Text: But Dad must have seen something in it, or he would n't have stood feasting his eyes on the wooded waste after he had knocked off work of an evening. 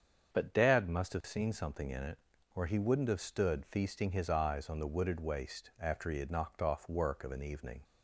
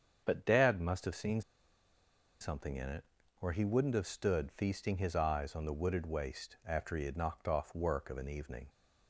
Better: first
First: starts louder than the rest; strong; until 1.3 s; 7 dB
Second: starts louder than the rest; strong; until 1.2 s; 7 dB // pauses between "seen" and "something"; at 1.4 s; 0.99 s long

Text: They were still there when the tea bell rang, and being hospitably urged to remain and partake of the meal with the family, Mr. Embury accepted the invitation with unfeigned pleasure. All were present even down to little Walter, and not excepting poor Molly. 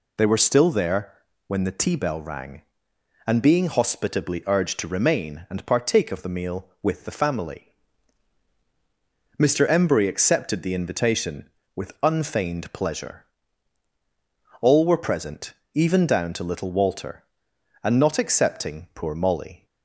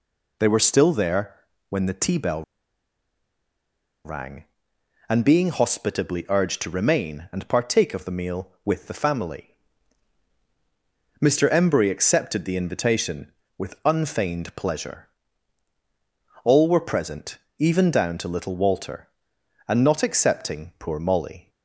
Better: first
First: pauses between "there" and "when"; slight; at 1.1 s; 0.34 s long // pauses between "present" and "even"; slight; at 15.5 s; 0.20 s long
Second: pauses between "there" and "when"; slight; at 1.3 s; 0.34 s long // pauses between "bell" and "rang"; strong; at 2.4 s; 1.6 s long // pauses between "present" and "even"; slight; at 17.3 s; 0.20 s long

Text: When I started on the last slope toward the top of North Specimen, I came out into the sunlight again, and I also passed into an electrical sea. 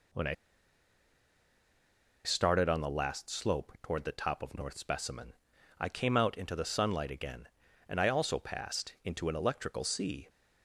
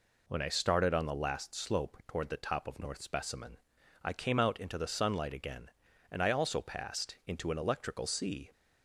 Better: second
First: pauses between "I" and "started"; strong; at 0.3 s; 1.9 s long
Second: none

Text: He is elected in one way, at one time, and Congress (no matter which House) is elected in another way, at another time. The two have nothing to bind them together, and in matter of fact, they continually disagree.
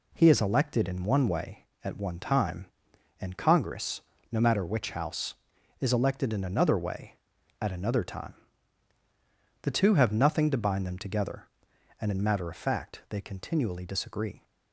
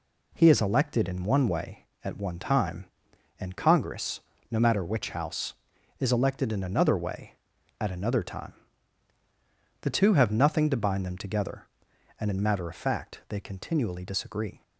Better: neither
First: none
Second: none

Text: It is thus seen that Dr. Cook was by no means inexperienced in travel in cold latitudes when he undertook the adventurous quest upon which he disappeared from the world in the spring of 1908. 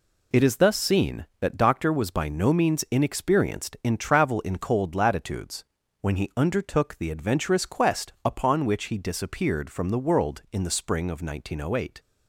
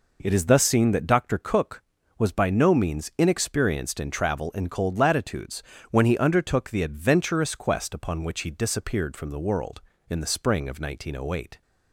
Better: second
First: skips "Cook"; at 1.9 s // pauses between "latitudes" and "when"; slight; at 5.6 s; 0.34 s long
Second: pauses between "latitudes" and "when"; slight; at 5.6 s; 0.26 s long

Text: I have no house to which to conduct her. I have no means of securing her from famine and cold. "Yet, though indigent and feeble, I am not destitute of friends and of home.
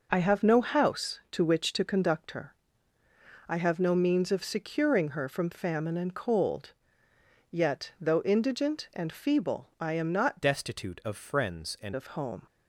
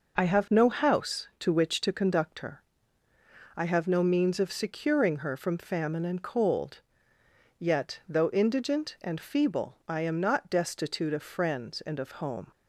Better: second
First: changes voice from "destitute" to "and"; from 10.4 to 11.9 s; 1.5 s long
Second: none

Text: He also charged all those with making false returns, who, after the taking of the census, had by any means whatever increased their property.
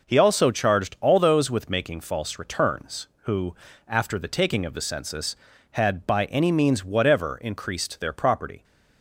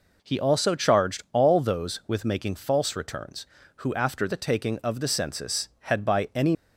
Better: first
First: none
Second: stops before "means whatever increased their property"; at 6.5 s

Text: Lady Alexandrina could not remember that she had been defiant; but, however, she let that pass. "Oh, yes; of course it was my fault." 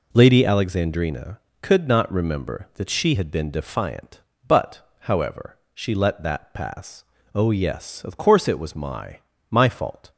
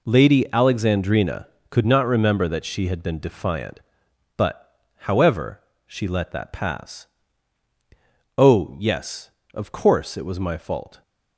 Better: second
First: says "my" twice; at 9.4 s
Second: none

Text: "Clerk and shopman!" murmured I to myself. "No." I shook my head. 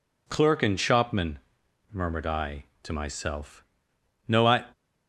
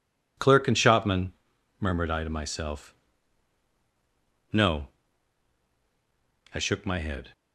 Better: second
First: stops before "shook my head"; at 4.7 s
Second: none

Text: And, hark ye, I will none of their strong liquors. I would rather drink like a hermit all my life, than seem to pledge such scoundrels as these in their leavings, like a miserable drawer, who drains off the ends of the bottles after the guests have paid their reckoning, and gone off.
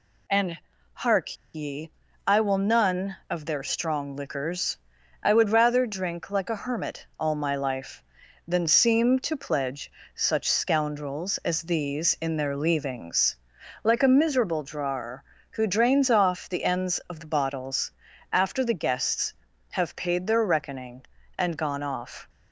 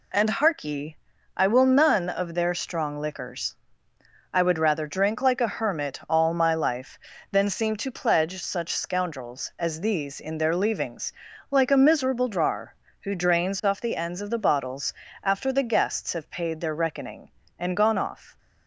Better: second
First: pauses between "hark" and "ye"; slight; at 1.3 s; 0.18 s long // pauses between "pledge" and "such"; slight; at 9.9 s; 0.24 s long // pauses between "bottles" and "after"; at 17.9 s; 0.40 s long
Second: pauses between "bottles" and "after"; slight; at 14.9 s; 0.28 s long

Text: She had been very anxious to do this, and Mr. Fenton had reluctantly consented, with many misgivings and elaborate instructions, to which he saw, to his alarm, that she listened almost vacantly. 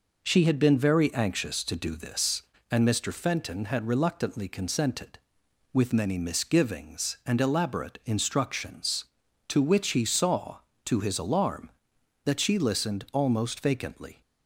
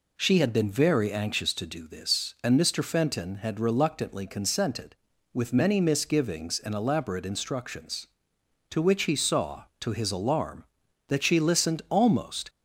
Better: first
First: none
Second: stops before "vacantly"; at 12.4 s

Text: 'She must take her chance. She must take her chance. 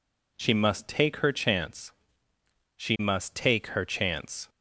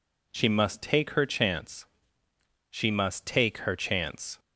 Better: neither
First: none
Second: none

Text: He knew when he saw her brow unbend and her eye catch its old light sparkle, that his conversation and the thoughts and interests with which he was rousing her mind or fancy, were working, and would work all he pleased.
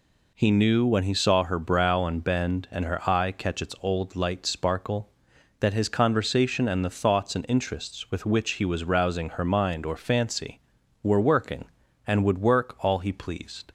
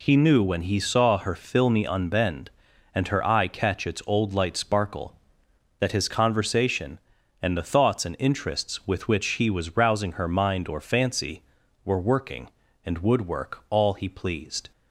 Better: first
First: none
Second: says "filmy" for "brow"; at 1.3 s

